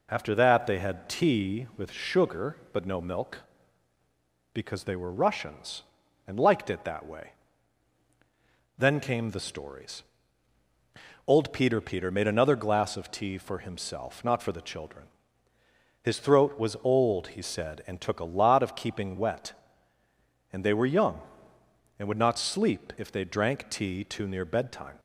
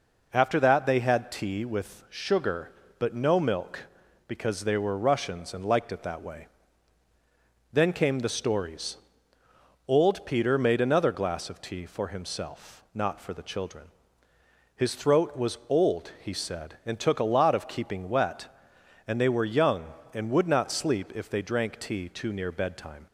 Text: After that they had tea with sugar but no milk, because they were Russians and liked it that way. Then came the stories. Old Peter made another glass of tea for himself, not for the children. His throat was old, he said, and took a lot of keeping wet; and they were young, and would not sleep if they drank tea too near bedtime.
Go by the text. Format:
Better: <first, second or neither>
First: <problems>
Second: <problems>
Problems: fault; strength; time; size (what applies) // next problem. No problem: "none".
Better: second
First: says "Peter" twice; at 11.7 s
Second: none